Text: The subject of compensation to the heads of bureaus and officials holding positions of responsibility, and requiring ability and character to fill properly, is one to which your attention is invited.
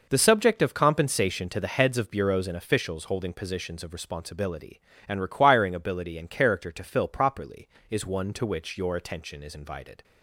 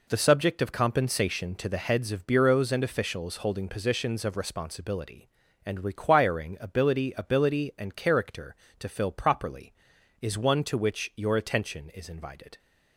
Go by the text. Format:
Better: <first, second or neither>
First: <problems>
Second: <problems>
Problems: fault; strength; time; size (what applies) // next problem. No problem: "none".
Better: first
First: none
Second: says "ability" twice; at 7.1 s